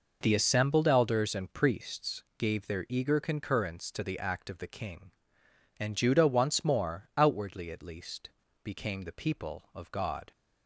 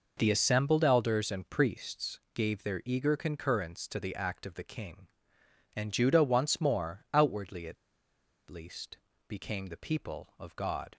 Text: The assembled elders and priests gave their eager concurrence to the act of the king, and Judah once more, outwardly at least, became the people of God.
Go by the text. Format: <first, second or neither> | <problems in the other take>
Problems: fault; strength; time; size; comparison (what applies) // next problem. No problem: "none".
first | pauses between "priests" and "gave"; slight; at 2.1 s; 0.16 s long; slight in the first // pauses between "at" and "least"; noticeable; at 7.7 s; 0.74 s long